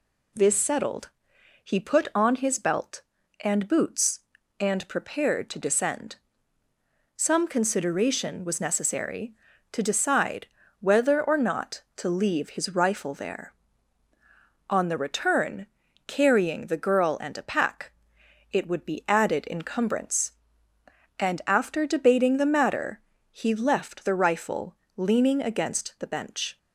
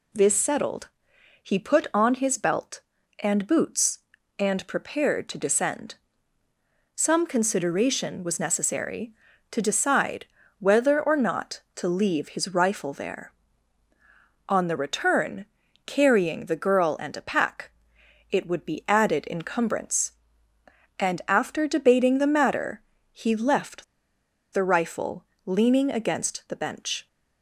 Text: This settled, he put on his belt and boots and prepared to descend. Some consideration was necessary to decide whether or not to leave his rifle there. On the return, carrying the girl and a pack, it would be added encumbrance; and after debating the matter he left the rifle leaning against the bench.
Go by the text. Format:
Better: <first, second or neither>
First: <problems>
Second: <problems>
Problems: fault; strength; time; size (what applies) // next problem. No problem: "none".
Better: first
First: pauses between "decide" and "whether"; slight; at 10.4 s; 0.32 s long // pauses between "matter" and "he"; slight; at 22.9 s; 0.30 s long // pauses between "rifle" and "leaning"; slight; at 24.7 s; 0.20 s long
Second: pauses between "decide" and "whether"; slight; at 10.2 s; 0.32 s long // pauses between "matter" and "he"; slight; at 22.8 s; 0.30 s long // pauses between "left" and "the"; noticeable; at 23.8 s; 0.68 s long // pauses between "rifle" and "leaning"; slight; at 25.2 s; 0.20 s long